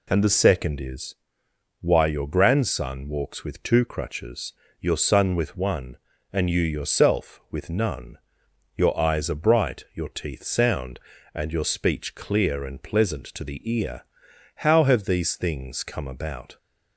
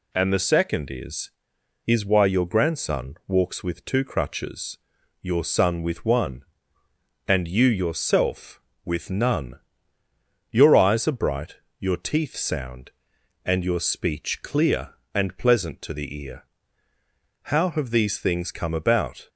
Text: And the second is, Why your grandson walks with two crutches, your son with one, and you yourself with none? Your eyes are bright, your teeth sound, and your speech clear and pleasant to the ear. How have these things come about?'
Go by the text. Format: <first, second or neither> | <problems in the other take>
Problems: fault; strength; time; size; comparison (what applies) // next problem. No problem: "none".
first | says "is" twice; at 1.8 s